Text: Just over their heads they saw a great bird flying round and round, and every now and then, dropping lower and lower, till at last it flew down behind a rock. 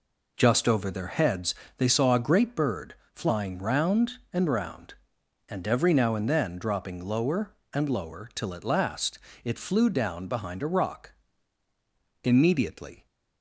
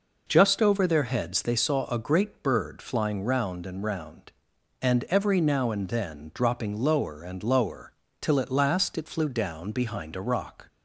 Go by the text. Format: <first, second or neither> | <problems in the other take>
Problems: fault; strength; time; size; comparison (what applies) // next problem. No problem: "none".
second | pauses between "heads" and "they"; slight; at 1.5 s; 0.24 s long // pauses between "bird" and "flying"; slight; at 2.9 s; 0.20 s long // pauses between "last" and "it"; slight; at 9.1 s; 0.28 s long // goes on to say "Immediately"; noticeable; from 12.2 s on; 0.84 s long